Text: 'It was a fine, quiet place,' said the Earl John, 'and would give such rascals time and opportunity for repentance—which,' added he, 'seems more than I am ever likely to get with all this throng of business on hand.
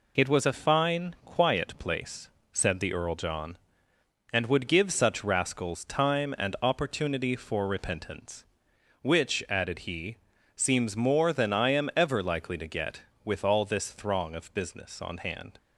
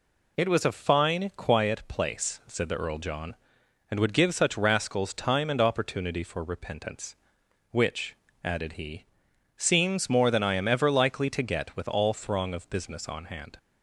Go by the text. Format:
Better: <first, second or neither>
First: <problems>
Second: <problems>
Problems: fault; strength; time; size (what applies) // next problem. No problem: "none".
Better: first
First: none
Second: skips "this"; at 12.1 s